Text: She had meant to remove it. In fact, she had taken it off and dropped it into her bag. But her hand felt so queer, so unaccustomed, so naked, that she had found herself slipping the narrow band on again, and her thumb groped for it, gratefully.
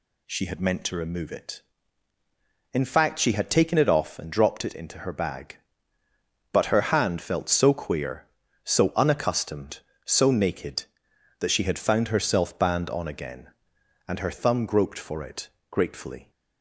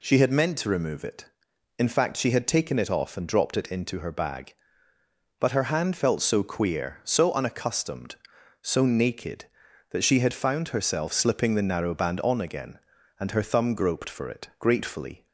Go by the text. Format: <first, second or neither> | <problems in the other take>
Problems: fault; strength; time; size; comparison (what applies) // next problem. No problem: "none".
second | skips "slipping the narrow"; at 12.5 s